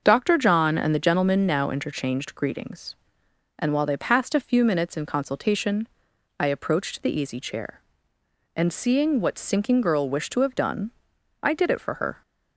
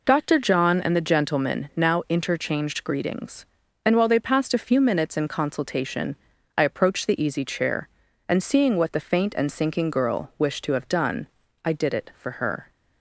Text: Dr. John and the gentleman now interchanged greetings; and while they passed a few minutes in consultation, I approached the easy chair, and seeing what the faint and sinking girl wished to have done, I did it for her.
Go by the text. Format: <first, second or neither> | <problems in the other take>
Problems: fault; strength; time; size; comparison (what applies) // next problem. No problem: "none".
second | starts louder than the rest; until 1.0 s; 6.5 dB // skips "the faint and"; at 9.3 s